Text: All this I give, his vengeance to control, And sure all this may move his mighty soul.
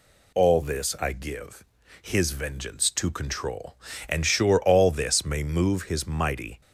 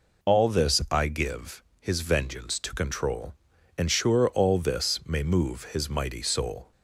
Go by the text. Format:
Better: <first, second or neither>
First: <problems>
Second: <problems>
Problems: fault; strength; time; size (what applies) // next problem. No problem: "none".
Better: second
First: stops before "soul"; at 6.6 s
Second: none